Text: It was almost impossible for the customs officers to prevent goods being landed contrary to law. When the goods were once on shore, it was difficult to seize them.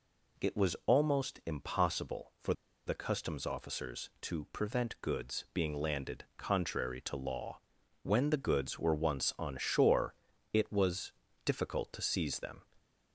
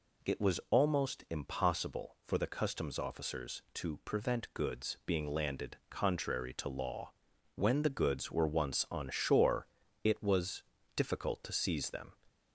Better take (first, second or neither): second